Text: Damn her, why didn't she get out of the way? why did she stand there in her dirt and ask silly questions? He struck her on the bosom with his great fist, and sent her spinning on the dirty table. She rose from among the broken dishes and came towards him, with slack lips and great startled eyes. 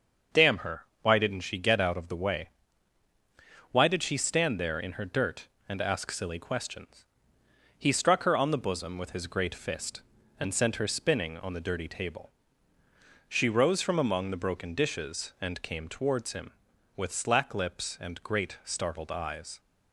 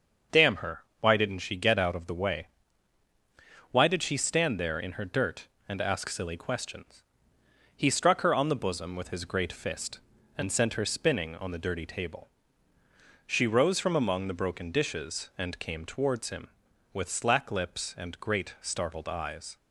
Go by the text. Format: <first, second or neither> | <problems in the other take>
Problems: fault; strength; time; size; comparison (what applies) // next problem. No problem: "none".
neither | starts louder than the rest; the same in both